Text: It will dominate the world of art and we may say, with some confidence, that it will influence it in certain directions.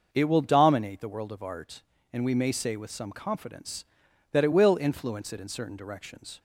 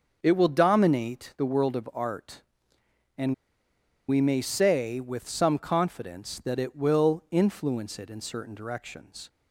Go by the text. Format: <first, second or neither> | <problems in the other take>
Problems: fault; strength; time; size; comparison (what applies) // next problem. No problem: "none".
first | starts louder than the rest; until 1.2 s; 6.5 dB // pauses between "and" and "we"; noticeable; at 3.3 s; 0.74 s long